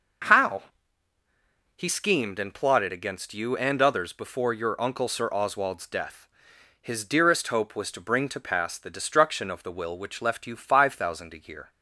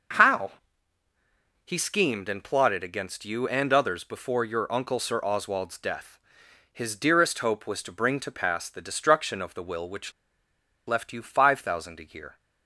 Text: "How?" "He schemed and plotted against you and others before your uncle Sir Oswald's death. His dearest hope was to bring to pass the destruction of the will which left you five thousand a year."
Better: first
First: none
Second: pauses between "which" and "left"; noticeable; at 10.1 s; 0.75 s long

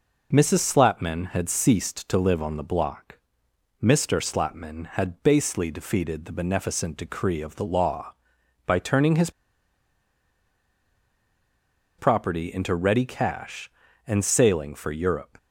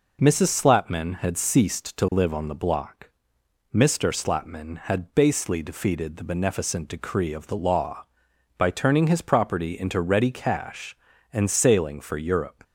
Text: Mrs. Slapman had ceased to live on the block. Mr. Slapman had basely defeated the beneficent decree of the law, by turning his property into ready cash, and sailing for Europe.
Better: second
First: pauses between "his" and "property"; strong; at 9.2 s; 2.6 s long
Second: none

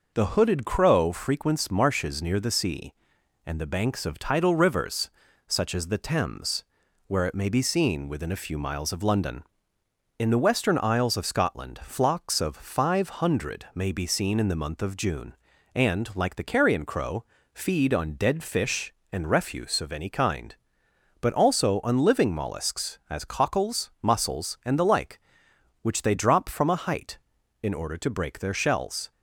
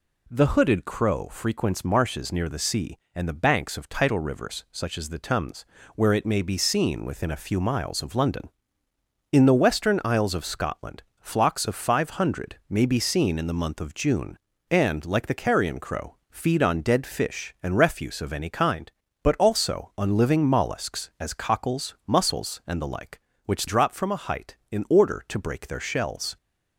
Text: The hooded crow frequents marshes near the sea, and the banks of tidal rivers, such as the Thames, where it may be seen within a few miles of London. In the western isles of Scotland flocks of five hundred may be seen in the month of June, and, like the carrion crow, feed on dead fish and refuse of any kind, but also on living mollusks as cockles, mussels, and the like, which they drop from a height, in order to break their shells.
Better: first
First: none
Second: pauses between "Scotland" and "flocks"; slight; at 11.0 s; 0.20 s long // skips "they"; at 23.6 s

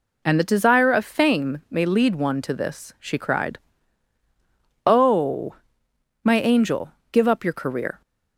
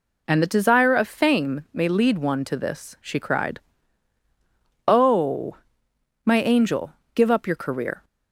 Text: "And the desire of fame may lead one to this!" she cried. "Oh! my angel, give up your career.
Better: neither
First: none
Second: none

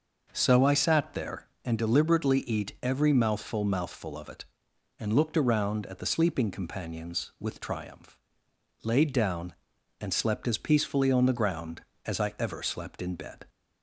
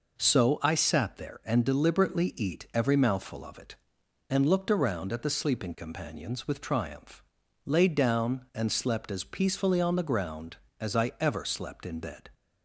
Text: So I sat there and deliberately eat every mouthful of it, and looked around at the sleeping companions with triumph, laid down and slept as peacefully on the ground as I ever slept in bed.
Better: second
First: says "mouthful" twice; at 3.6 s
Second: none

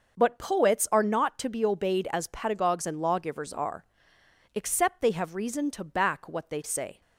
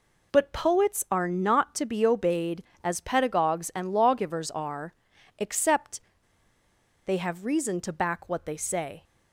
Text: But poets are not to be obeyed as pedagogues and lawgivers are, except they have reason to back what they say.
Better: first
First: none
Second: pauses between "except" and "they"; at 5.9 s; 1.0 s long

